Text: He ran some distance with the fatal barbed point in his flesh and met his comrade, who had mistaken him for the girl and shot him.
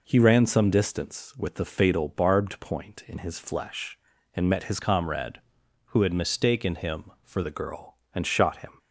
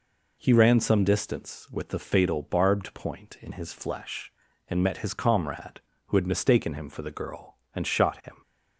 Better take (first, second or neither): second